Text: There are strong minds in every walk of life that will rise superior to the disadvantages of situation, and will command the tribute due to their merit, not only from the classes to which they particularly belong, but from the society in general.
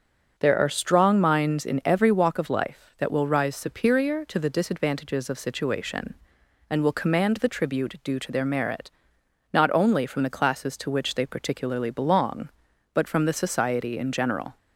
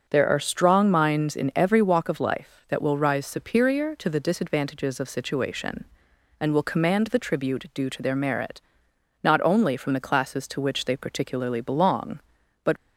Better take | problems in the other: first | starts louder than the rest; until 1.0 s; 6.5 dB; also in the first // stops before "from the society in general"; at 12.7 s

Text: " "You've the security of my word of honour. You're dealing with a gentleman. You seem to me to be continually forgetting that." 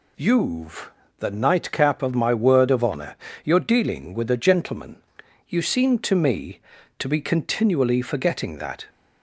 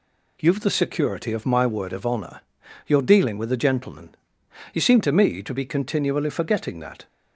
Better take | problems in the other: second | pauses between "You've" and "the"; slight; at 0.9 s; 0.26 s long // says "nightcap" for "security"; at 1.2 s

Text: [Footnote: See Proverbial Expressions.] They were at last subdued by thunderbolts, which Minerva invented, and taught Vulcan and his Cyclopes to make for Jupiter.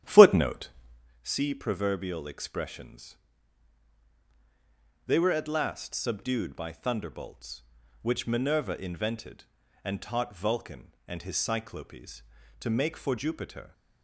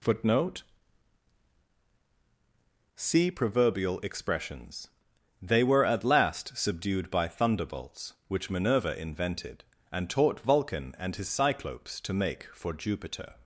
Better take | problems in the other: second | starts louder than the rest; strong; until 1.1 s; 11 dB

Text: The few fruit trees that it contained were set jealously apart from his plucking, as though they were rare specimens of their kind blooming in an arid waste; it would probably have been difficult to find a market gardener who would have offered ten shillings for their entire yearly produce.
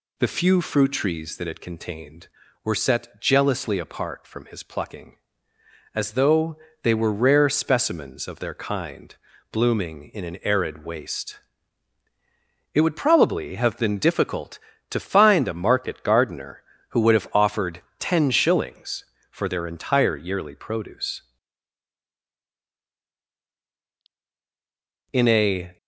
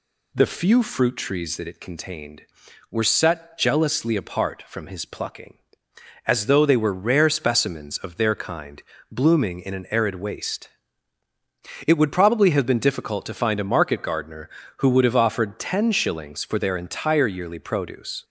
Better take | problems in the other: second | pauses between "though" and "they"; slight; at 6.5 s; 0.26 s long // pauses between "kind" and "blooming"; slight; at 9.1 s; 0.36 s long; slight in the second // pauses between "offered" and "ten"; slight; at 17.8 s; 0.18 s long // goes on to say "In a"; noticeable; from 25.1 s on; 0.64 s long

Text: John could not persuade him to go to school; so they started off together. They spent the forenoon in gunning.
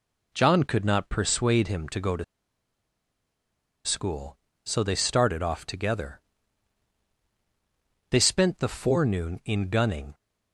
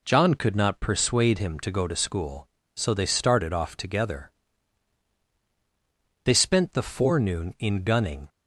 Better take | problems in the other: second | pauses between "to" and "school"; strong; at 2.2 s; 1.6 s long

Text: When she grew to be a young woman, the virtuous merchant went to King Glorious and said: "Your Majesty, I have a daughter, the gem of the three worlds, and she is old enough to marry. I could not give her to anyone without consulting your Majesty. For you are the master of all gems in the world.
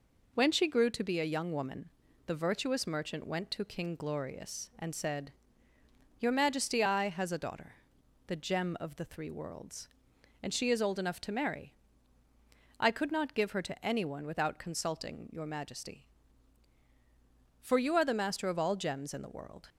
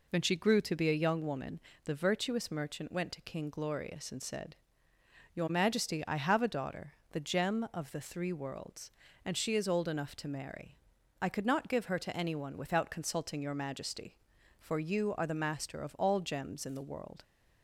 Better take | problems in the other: second | says "has" for "have"; at 7.1 s

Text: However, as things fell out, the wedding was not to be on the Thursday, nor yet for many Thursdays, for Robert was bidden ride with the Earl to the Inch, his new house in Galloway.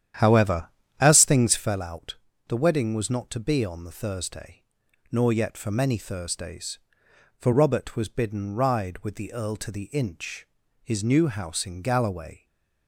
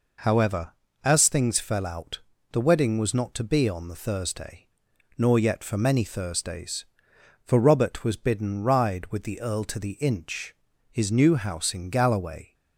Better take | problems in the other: second | starts louder than the rest; strong; until 1.9 s; 10 dB // stays silent after the last word; slight; from 12.3 s on; 0.5 s long

